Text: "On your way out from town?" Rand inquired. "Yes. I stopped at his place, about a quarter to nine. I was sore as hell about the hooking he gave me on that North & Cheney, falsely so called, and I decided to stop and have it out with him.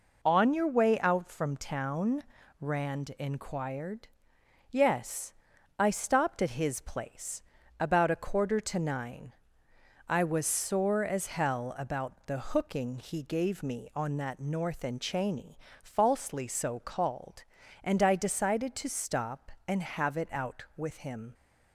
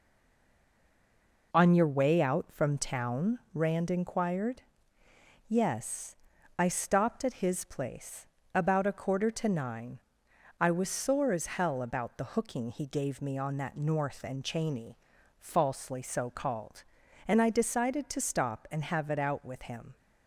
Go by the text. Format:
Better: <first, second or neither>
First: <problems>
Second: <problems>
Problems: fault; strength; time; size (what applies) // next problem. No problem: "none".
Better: first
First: none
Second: stays silent before the first word; noticeable; until 1.5 s; 1.5 s long